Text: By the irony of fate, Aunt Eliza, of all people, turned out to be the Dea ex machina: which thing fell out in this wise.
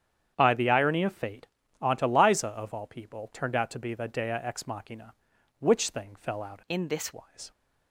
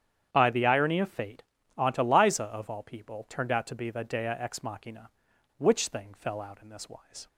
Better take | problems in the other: second | starts louder than the rest; strong; until 1.3 s; 9 dB; strong in the second // changes voice from "in" to "this"; from 6.7 to 7.1 s; 0.4 s long

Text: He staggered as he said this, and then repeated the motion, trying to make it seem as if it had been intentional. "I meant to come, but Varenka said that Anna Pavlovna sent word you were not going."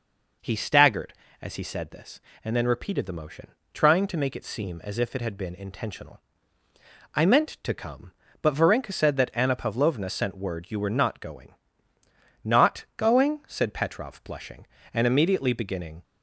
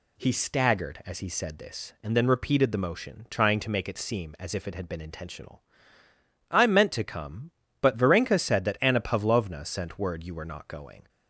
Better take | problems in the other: second | goes on to say "Not going said Petrov blushing and immediately beginning"; strong; from 12.4 s on; 3.5 s long

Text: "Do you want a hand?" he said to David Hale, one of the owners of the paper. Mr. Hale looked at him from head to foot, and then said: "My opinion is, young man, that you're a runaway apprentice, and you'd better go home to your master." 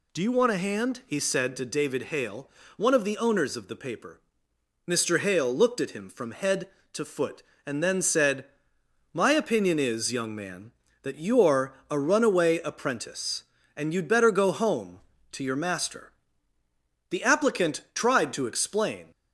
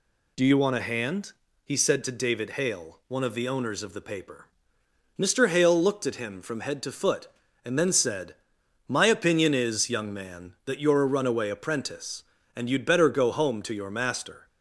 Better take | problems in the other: second | pauses between "you're" and "a"; slight; at 11.7 s; 0.16 s long // goes on to say "The applicant tried to explain"; strong; from 17.0 s on; 2.0 s long

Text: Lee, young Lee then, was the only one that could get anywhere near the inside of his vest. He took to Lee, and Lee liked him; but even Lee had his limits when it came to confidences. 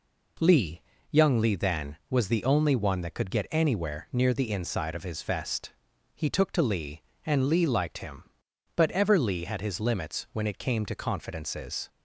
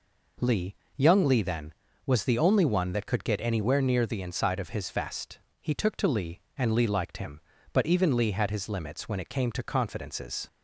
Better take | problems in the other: second | says "ever" for "even"; at 8.9 s

